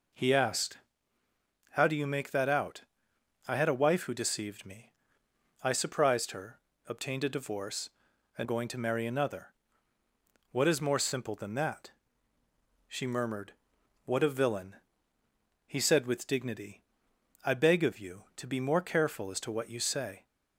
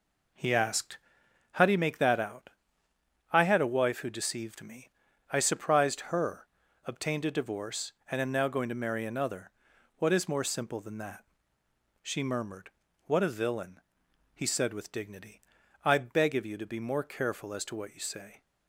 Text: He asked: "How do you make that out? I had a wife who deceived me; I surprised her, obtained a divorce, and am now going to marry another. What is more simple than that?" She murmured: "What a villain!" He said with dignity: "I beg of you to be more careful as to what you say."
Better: second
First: skips "am now"; at 8.4 s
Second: none

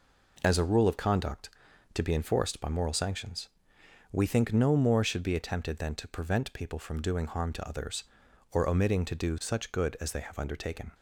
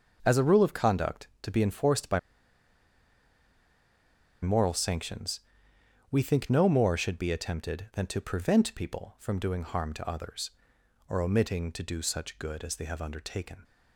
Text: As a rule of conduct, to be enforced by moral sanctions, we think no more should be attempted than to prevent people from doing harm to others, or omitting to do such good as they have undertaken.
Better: first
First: none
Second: starts louder than the rest; noticeable; until 1.2 s; 6 dB // pauses between "by" and "moral"; strong; at 2.1 s; 2.2 s long

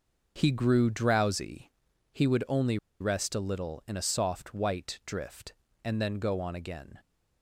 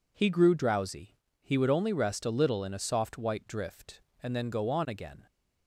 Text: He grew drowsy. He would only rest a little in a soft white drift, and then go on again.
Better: second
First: pauses between "only" and "rest"; slight; at 2.7 s; 0.23 s long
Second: none

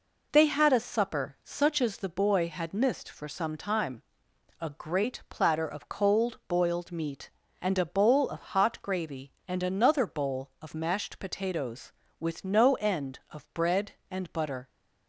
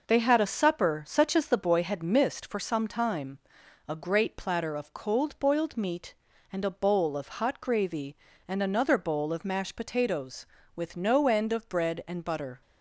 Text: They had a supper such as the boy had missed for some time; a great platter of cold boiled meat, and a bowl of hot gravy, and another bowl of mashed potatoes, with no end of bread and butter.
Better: neither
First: none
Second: none

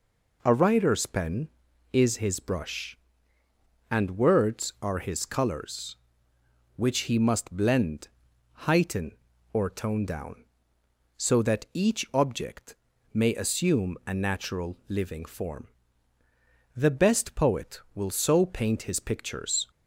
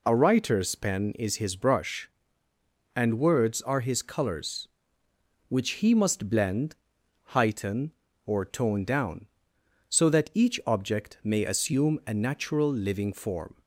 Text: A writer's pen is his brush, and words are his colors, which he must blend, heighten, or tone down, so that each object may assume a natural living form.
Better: second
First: pauses between "object" and "may"; at 12.7 s; 0.38 s long // goes on to say "The best poet will so paint his pictures"; strong; from 16.7 s on; 2.9 s long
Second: none

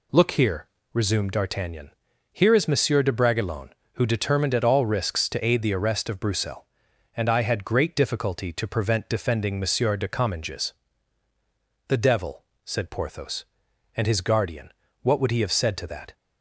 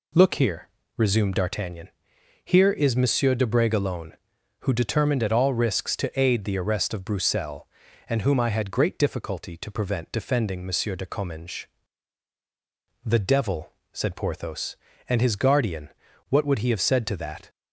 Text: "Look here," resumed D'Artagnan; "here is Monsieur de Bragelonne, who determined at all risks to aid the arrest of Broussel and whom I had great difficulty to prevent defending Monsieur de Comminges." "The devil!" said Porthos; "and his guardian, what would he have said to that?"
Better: second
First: skips "whom"; at 7.2 s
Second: none

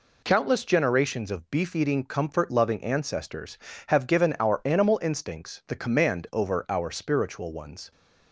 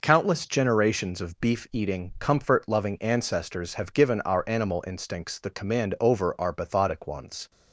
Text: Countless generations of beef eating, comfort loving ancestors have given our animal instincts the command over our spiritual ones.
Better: first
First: none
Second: says "bathotic" for "spiritual"; at 6.5 s

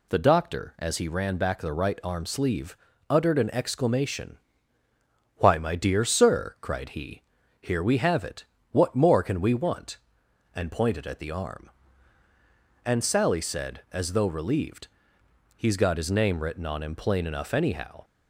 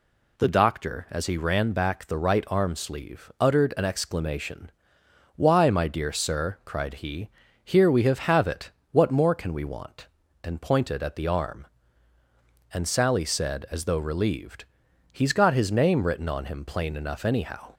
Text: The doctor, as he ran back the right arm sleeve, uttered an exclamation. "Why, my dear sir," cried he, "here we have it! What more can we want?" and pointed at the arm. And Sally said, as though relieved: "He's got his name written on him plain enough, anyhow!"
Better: first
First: none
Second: says "have" twice; at 8.1 s

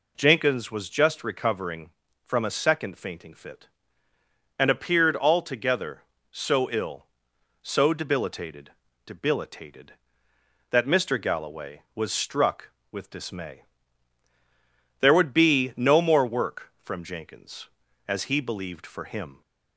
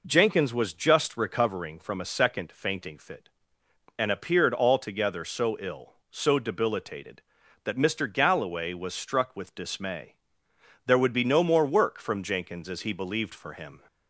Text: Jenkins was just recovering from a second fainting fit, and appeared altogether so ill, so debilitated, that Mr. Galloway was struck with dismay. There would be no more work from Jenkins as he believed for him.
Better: second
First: says "debilitated" twice; at 9.0 s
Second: none

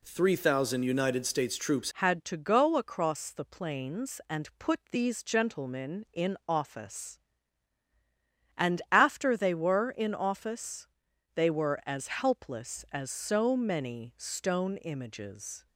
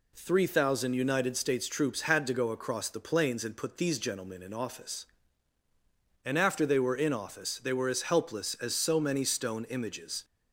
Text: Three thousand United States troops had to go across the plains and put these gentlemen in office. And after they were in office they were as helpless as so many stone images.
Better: second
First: changes voice at "had"; from 2.0 s on; 13.6 s long // pauses between "office" and "they"; noticeable; at 10.8 s; 0.48 s long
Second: none

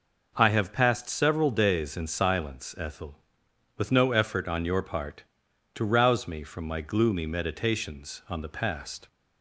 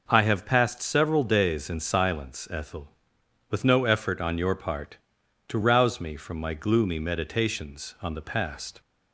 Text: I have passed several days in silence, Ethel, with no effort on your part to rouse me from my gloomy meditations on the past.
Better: neither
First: none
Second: none

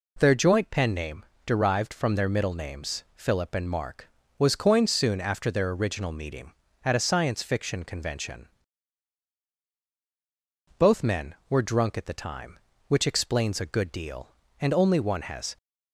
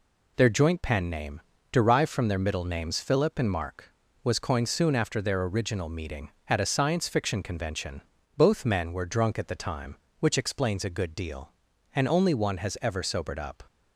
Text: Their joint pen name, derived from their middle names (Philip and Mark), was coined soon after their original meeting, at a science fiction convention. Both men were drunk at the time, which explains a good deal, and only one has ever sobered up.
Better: second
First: stops before "ever sobered up"; at 15.5 s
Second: none

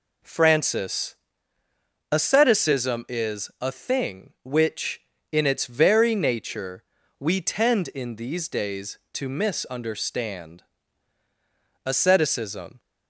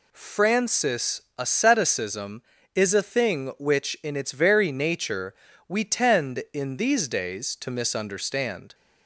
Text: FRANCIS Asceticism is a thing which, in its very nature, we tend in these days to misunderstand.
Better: second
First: pauses between "FRANCIS" and "Asceticism"; noticeable; at 1.1 s; 0.96 s long // goes on to say "Asceticism"; noticeable; from 11.8 s on; 0.94 s long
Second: pauses between "FRANCIS" and "Asceticism"; slight; at 1.2 s; 0.18 s long

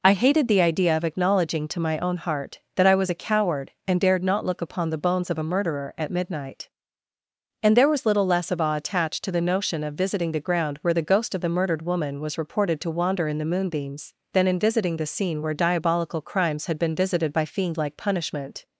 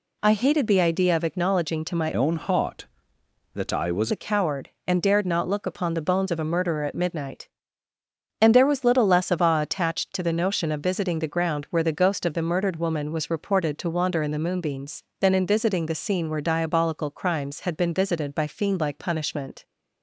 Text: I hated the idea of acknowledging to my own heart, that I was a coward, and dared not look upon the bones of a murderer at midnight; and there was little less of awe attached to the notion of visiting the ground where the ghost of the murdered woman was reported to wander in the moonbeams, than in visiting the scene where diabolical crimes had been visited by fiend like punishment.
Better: first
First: none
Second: changes voice from "own" to "was"; from 2.1 to 4.1 s; 2.0 s long

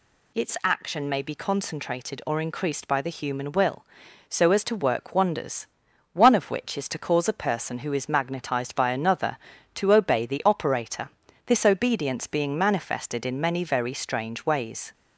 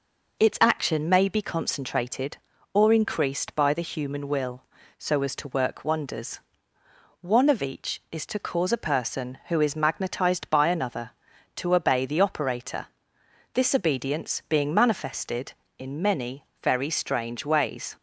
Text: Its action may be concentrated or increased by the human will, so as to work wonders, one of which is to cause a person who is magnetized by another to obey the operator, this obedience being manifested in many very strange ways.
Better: first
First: none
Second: says "each" for "which"; at 7.5 s // pauses between "many" and "very"; slight; at 16.4 s; 0.18 s long

